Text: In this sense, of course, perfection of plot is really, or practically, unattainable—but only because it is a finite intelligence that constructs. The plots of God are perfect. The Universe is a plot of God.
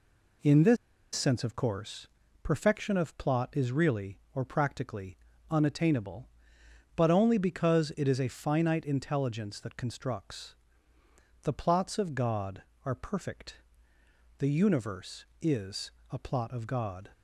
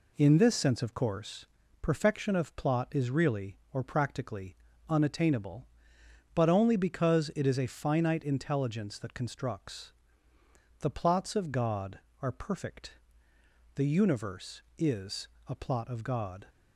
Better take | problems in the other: second | pauses between "this" and "sense"; at 0.7 s; 0.38 s long // pauses between "is" and "a"; slight; at 15.9 s; 0.20 s long; slight in the second

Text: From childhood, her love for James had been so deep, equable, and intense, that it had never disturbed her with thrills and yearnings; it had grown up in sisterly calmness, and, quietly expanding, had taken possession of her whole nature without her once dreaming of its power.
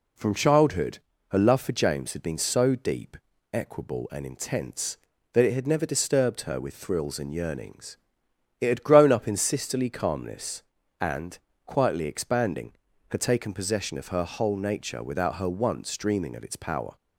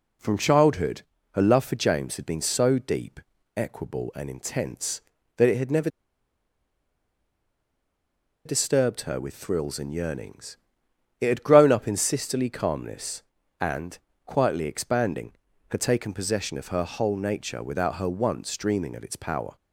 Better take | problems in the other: first | pauses between "never" and "disturbed"; strong; at 5.8 s; 2.5 s long

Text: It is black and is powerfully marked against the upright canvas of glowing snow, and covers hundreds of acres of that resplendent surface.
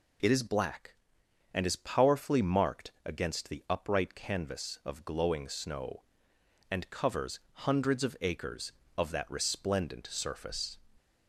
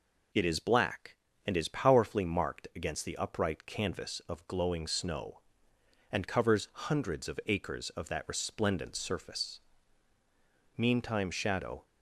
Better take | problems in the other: first | goes on to say "Meantime shadow"; noticeable; from 10.7 s on; 1.0 s long

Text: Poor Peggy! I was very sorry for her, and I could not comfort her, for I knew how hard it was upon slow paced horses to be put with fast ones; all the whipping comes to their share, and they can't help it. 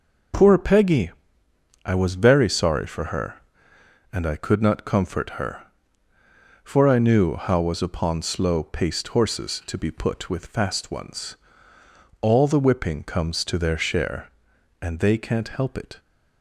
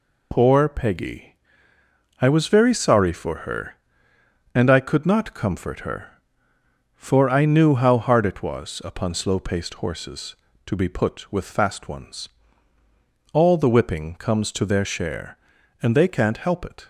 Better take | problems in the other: second | skips "hard it"; at 7.6 s

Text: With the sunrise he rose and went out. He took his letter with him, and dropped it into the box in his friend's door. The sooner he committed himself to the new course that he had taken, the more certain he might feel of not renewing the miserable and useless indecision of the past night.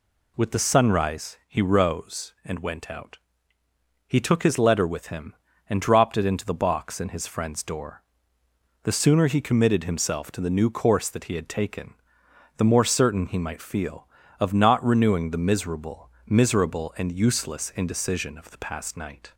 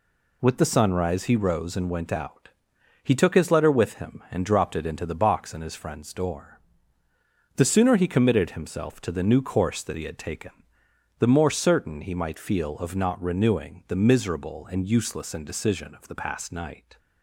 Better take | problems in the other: second | says "miserable" twice; at 16.2 s

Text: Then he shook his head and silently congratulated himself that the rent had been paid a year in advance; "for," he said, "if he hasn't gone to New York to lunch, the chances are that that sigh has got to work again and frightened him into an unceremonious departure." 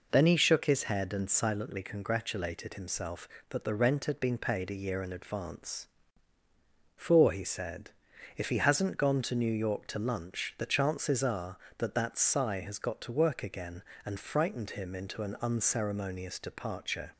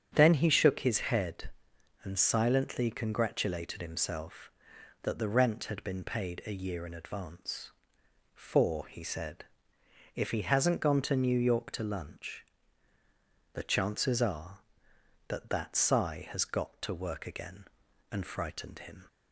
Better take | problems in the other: first | starts louder than the rest; strong; until 1.1 s; 8 dB // stops before "into an unceremonious departure"; at 19.0 s

